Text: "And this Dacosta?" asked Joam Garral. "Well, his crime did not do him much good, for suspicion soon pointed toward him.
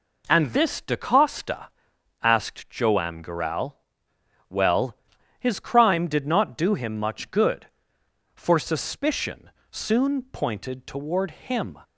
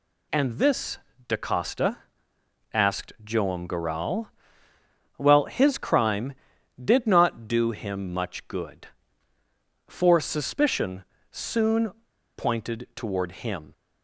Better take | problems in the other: first | pauses between "this" and "Dacosta"; slight; at 0.9 s; 0.28 s long // pauses between "suspicion" and "soon"; slight; at 11.0 s; 0.28 s long; slight in the first // pauses between "soon" and "pointed"; noticeable; at 11.8 s; 0.46 s long

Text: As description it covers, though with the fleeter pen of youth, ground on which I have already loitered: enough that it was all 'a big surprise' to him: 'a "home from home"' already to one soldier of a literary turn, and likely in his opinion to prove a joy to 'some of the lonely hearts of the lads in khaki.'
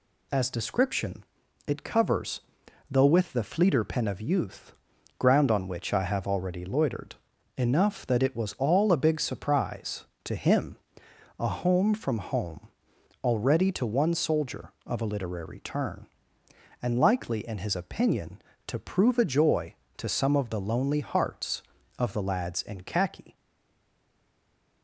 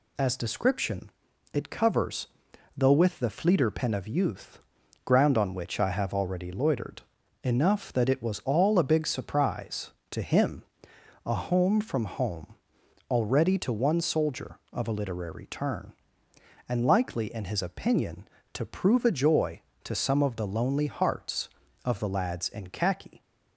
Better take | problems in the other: second | pauses between "description" and "it"; at 1.2 s; 0.42 s long; also in the second // pauses between "home" and "already"; noticeable; at 12.6 s; 0.56 s long; noticeable in the second // stays silent after the last word; noticeable; from 23.3 s on; 1.5 s long

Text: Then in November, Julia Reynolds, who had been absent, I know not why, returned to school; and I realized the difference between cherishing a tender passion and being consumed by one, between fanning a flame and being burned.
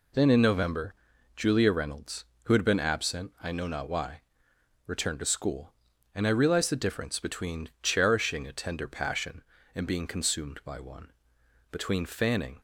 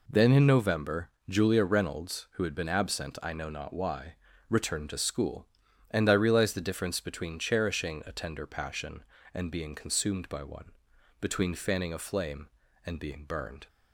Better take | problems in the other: second | stops before "a flame and being burned"; at 12.5 s

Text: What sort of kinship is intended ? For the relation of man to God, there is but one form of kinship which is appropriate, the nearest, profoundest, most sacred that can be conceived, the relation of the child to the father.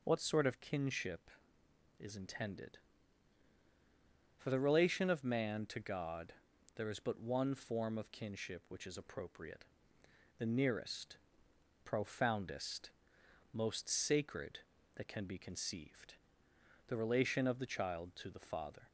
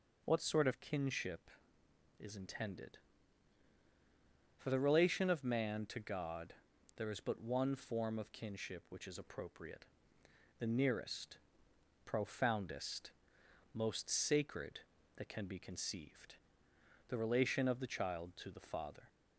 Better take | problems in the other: neither | none

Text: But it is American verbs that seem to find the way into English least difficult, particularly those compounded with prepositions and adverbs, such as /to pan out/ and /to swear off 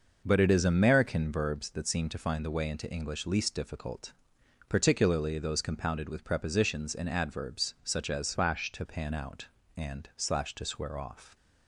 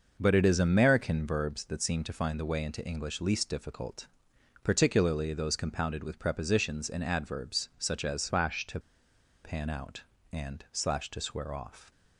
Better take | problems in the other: first | pauses between "to" and "pan"; noticeable; at 8.7 s; 0.65 s long

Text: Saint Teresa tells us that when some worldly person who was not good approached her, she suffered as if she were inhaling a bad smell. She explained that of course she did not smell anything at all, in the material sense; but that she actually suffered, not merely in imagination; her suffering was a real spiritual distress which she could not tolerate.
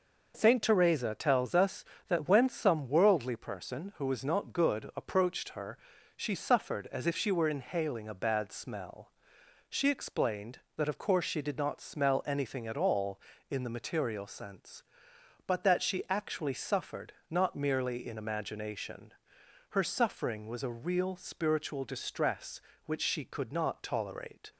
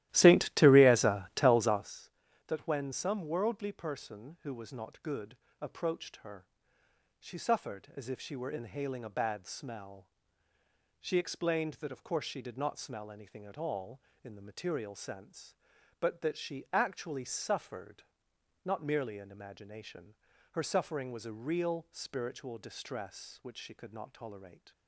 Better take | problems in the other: first | starts louder than the rest; strong; until 2.0 s; 14.5 dB // pauses between "good" and "approached"; slight; at 5.3 s; 0.24 s long

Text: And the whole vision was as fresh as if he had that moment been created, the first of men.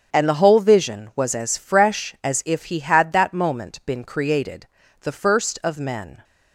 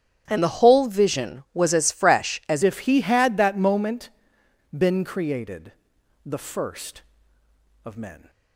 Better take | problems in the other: first | starts louder than the rest; strong; until 1.2 s; 10 dB; strong in the first // changes voice at "if"; from 2.6 s on; 5.6 s long // pauses between "moment" and "been"; noticeable; at 4.0 s; 0.66 s long

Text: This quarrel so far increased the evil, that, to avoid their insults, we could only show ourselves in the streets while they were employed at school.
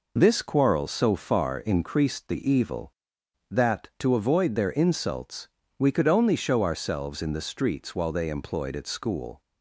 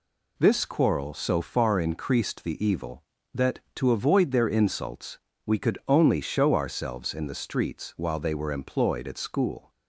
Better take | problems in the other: second | skips "were"; at 8.2 s

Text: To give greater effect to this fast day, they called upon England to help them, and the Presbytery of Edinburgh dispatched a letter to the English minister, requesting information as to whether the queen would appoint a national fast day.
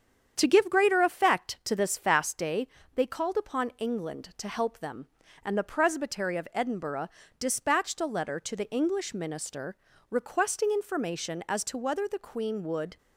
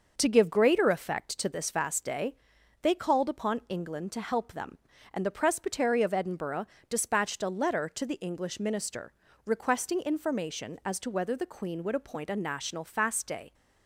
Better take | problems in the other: second | starts louder than the rest; strong; until 1.3 s; 8 dB; noticeable in the second // pauses between "Edinburgh" and "dispatched"; slight; at 7.0 s; 0.32 s long; slight in the second // stops before "appoint a national fast day"; at 12.9 s

